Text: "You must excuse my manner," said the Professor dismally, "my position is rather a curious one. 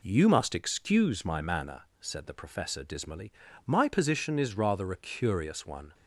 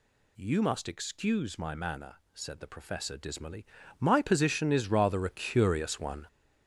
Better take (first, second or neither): first